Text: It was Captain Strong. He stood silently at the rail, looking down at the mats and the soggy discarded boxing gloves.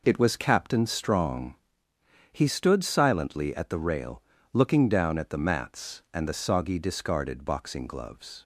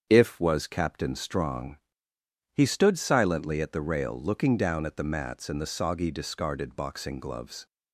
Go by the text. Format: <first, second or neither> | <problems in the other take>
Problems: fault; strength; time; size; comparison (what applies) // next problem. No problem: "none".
first | starts louder than the rest; strong; until 1.1 s; 7.5 dB // says "If" for "It"; at 0.0 s